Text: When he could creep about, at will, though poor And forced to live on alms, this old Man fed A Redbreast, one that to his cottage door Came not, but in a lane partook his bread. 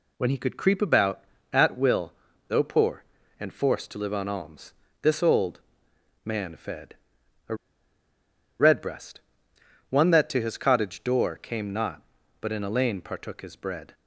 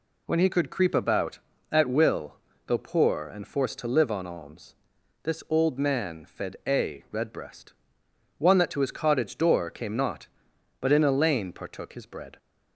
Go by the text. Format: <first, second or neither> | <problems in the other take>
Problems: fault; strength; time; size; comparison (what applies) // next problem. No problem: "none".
second | pauses between "old" and "Man"; noticeable; at 5.5 s; 0.64 s long // pauses between "fed" and "A"; noticeable; at 6.9 s; 0.54 s long // pauses between "A" and "Redbreast"; at 7.5 s; 1.0 s long